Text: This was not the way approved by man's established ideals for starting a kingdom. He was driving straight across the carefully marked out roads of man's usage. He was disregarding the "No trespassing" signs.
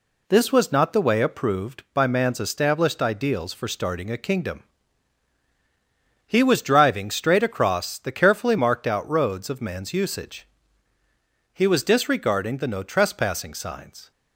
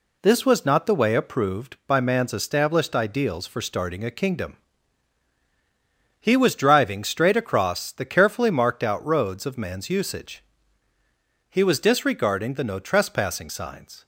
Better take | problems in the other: neither | none

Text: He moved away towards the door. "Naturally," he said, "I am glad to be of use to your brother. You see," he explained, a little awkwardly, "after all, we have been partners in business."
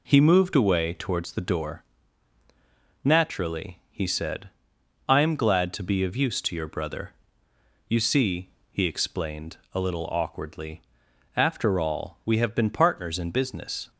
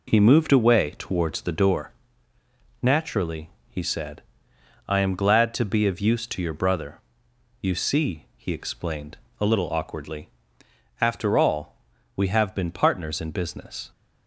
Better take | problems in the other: neither | none

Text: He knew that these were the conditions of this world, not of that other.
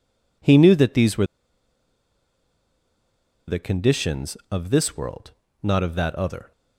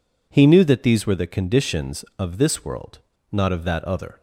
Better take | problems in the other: second | pauses between "were" and "the"; strong; at 1.2 s; 2.2 s long

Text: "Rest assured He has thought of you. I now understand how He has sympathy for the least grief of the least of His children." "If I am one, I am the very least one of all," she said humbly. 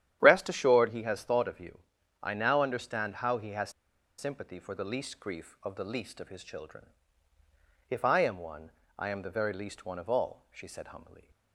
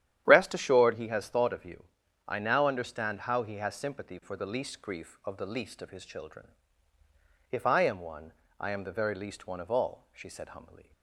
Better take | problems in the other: second | starts louder than the rest; strong; until 1.2 s; 10.5 dB; strong in the second // pauses between "has" and "sympathy"; noticeable; at 3.7 s; 0.48 s long

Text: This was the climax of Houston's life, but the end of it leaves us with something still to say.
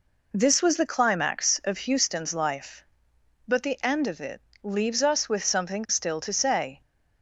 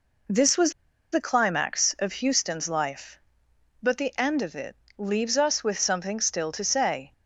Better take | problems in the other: first | pauses between "was" and "the"; at 0.7 s; 0.39 s long // pauses between "it" and "leaves"; slight; at 4.7 s; 0.24 s long; slight in the first

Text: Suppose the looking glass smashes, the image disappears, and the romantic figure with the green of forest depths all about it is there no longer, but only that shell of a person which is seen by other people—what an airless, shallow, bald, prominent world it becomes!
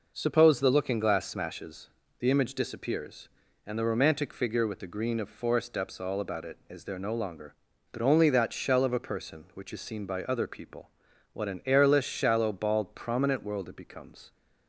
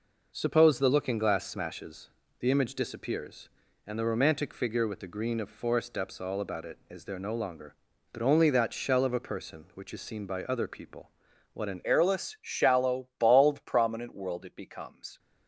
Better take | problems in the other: first | changes voice at "airless"; from 11.8 s on; 3.3 s long

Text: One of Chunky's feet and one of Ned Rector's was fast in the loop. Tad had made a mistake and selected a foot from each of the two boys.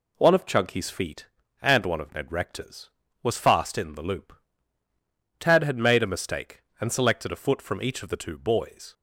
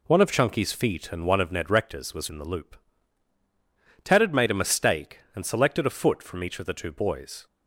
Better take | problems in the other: first | skips "fast"; at 2.2 s

